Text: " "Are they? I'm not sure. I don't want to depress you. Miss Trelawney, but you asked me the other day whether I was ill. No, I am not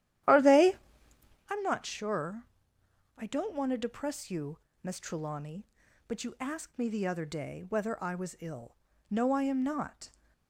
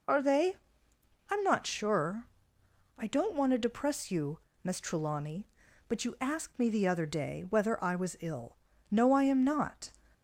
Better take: second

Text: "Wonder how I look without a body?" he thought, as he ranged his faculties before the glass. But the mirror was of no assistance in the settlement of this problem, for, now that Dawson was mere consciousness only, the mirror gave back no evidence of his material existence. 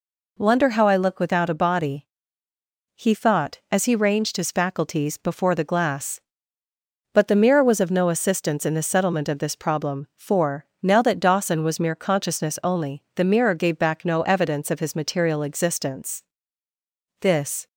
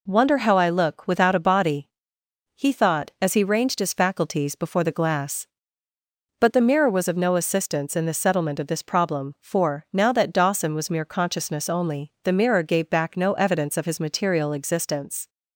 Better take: second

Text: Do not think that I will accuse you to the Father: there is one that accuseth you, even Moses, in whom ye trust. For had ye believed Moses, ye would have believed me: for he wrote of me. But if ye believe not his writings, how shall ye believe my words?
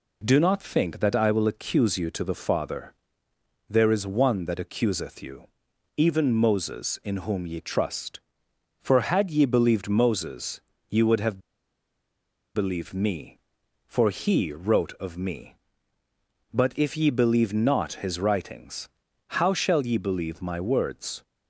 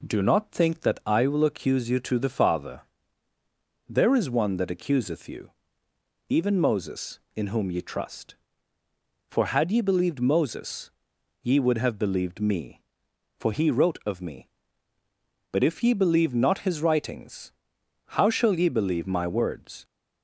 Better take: second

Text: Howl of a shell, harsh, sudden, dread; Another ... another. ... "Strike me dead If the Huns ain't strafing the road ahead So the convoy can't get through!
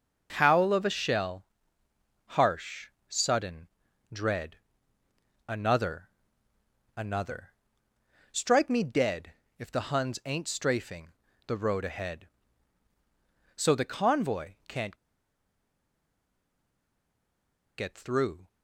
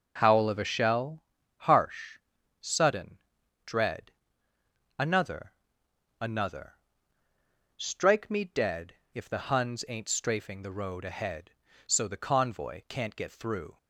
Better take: second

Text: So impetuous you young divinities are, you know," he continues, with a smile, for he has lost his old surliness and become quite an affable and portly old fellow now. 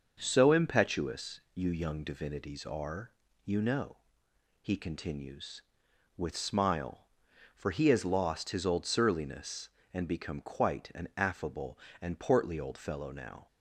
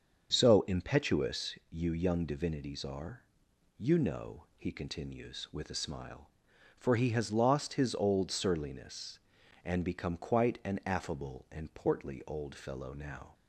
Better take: second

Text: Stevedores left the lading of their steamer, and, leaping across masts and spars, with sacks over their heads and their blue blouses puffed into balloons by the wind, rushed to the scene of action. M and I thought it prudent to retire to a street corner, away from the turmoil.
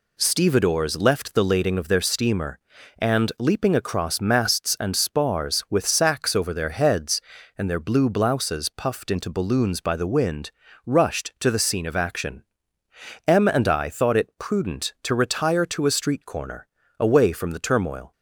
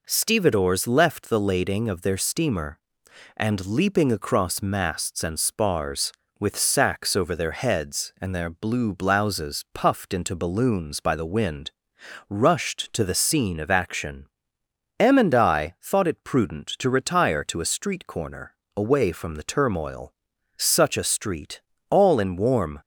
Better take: first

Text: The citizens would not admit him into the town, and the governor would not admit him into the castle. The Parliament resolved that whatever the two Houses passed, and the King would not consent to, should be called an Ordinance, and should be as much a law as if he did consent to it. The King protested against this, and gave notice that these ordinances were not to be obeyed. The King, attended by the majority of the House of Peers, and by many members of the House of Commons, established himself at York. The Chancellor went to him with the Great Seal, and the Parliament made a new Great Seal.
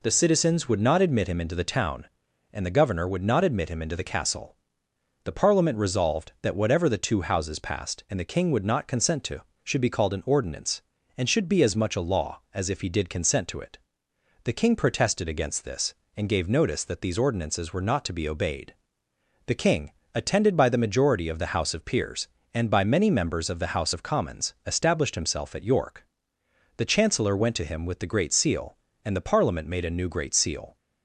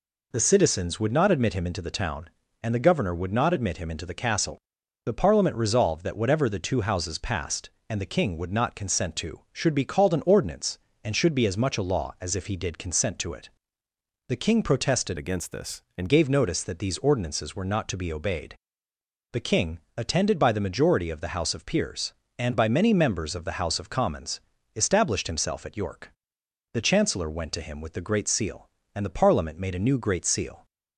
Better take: first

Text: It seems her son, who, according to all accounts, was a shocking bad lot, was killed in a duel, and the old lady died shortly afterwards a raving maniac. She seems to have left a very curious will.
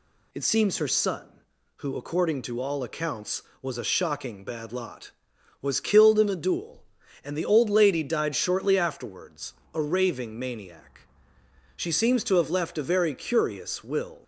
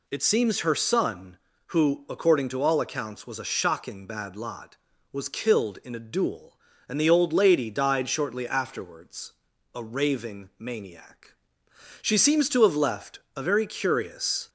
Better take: first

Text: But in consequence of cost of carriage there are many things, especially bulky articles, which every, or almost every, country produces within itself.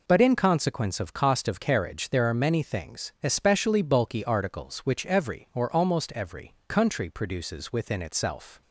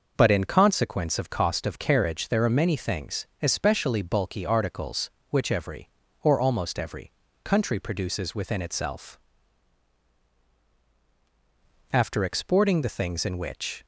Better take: first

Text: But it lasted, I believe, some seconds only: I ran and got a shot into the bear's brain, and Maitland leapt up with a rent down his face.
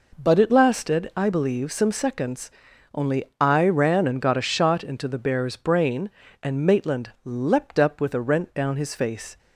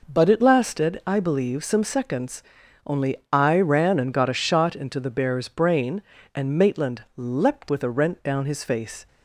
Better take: first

